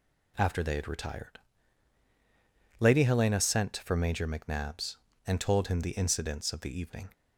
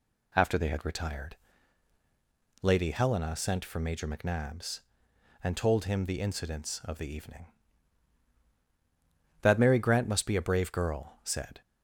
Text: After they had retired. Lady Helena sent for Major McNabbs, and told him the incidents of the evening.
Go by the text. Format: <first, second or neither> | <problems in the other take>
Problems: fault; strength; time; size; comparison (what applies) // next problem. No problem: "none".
first | goes on to say "That Mary Grant must be a brave girl said"; strong; from 9.4 s on; 2.1 s long